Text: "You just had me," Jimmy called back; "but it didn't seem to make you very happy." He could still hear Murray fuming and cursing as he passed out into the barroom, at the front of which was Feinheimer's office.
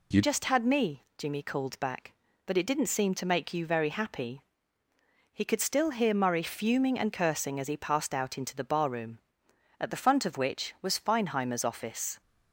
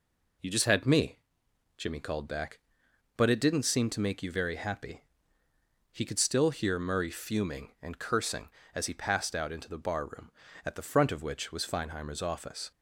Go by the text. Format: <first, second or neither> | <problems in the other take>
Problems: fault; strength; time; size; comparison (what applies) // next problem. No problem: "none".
second | changes voice at "just"; from 0.2 s on; 11.9 s long